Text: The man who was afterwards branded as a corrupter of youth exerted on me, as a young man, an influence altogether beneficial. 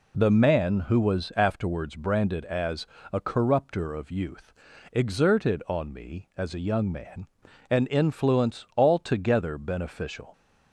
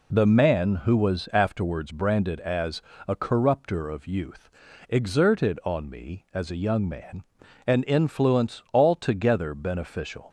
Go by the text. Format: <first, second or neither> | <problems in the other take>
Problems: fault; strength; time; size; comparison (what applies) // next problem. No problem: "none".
neither | pauses between "as" and "a"; slight; the same in both // pauses between "youth" and "exerted"; the same in both